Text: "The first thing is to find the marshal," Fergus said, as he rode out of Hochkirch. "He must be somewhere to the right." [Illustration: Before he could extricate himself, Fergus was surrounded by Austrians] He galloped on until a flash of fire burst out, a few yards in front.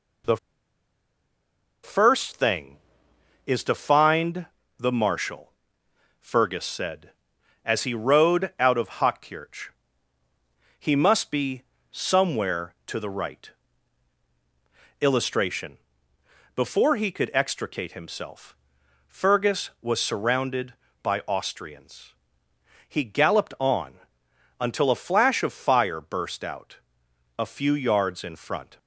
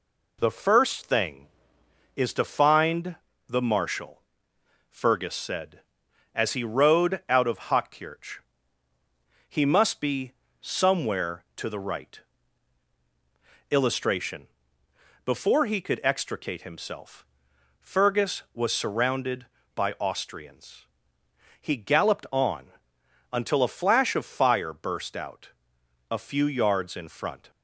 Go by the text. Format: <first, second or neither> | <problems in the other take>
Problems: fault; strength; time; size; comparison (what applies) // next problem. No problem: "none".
second | pauses between "The" and "first"; strong; at 0.3 s; 1.4 s long // pauses between "find" and "the"; slight; at 4.4 s; 0.30 s long; slight in the second // pauses between "be" and "somewhere"; slight; at 11.6 s; 0.30 s long; slight in the second // pauses between "Austrians" and "He"; noticeable; at 22.1 s; 0.74 s long; noticeable in the second // pauses between "on" and "until"; noticeable; at 23.9 s; 0.60 s long; noticeable in the second